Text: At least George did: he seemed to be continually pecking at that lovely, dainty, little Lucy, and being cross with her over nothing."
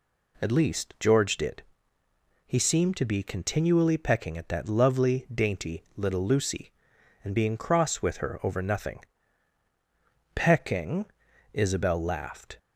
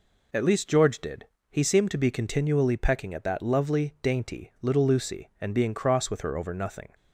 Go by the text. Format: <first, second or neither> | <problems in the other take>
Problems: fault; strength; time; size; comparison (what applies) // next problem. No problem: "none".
second | goes on to say "Pecking Isabel laughed"; strong; from 10.3 s on; 2.2 s long